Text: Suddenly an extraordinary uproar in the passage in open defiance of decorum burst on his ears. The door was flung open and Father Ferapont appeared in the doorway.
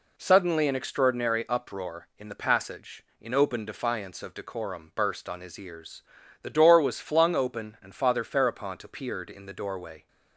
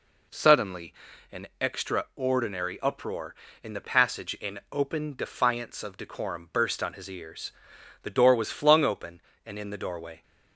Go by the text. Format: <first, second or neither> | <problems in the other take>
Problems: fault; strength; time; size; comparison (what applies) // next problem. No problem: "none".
first | pauses between "Suddenly" and "an"; at 0.9 s; 0.38 s long // skips "Father Ferapont appeared"; at 9.5 s